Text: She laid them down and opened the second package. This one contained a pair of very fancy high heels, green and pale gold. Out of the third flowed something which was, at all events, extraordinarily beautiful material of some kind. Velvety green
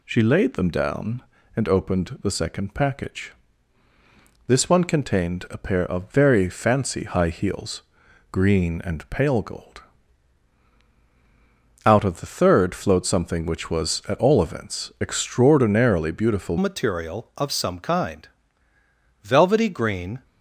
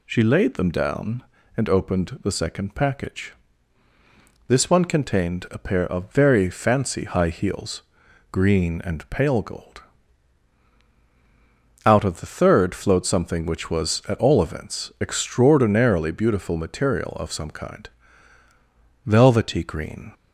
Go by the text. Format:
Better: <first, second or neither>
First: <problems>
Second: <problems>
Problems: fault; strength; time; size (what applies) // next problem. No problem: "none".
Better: second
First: changes voice at "material"; from 16.5 s on; 3.7 s long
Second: none